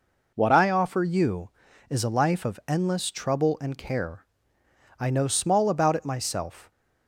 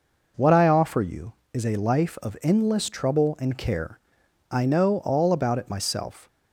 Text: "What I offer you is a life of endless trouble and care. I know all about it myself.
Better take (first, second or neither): second